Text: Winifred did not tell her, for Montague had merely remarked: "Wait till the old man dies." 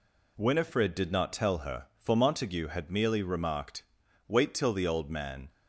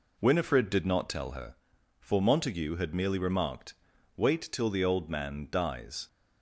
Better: second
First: stops before "dies"; at 5.4 s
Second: none

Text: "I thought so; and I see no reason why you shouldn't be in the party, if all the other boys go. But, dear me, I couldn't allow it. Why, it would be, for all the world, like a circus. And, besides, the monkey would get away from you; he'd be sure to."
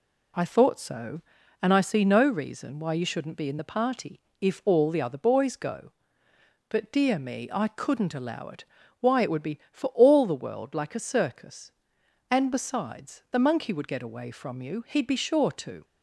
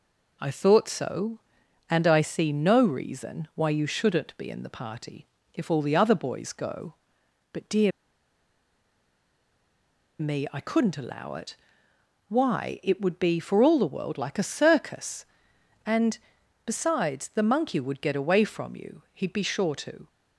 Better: first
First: none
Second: pauses between "dear" and "me"; strong; at 7.9 s; 2.2 s long

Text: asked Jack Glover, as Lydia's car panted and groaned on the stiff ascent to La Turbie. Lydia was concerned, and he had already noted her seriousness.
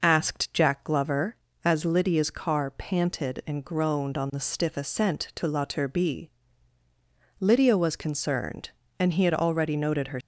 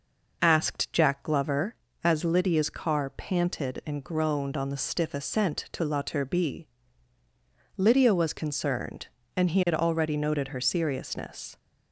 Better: second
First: stops before "seriousness"; at 10.2 s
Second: none

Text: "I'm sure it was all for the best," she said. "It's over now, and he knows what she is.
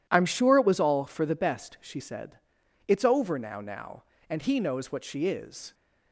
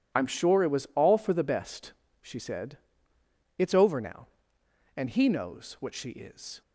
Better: second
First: says "now" twice; at 3.5 s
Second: none

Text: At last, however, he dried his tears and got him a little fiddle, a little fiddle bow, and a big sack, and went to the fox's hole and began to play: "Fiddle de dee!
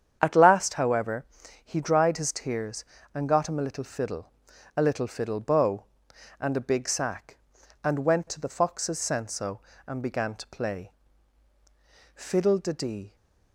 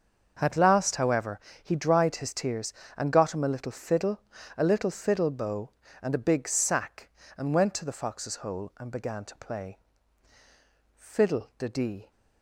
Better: second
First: starts louder than the rest; strong; until 1.2 s; 8.5 dB // says "senso" for "hole"; at 8.9 s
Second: starts louder than the rest; until 1.4 s; 6.5 dB

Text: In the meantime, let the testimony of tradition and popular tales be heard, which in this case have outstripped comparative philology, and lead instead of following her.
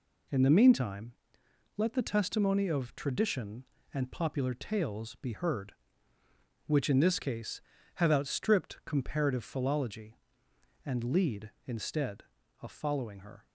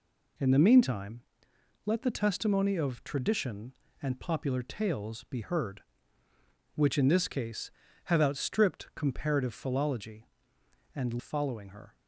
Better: first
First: none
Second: skips "lead instead of"; at 11.2 s

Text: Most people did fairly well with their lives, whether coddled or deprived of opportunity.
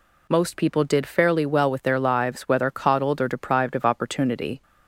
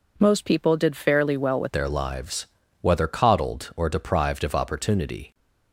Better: first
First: none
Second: changes voice at "their"; from 1.7 s on; 3.6 s long

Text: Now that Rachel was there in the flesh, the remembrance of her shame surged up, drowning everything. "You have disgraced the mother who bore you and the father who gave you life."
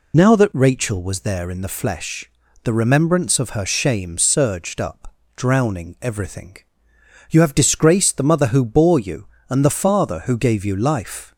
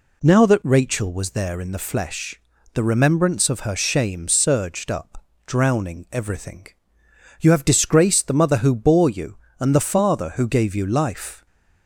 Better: second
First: loses the start of "Now"; at 0.1 s; 30 ms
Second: none

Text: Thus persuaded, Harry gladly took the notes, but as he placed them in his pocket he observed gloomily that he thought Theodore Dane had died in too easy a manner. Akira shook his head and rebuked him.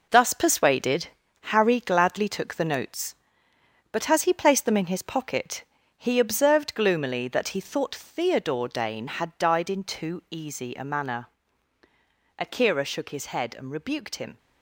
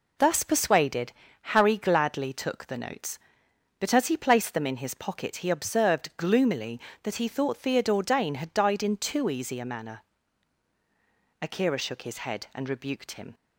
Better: second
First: gets quieter; strong; throughout; 8.5 dB // pauses between "pocket" and "he"; slight; at 5.6 s; 0.34 s long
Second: none

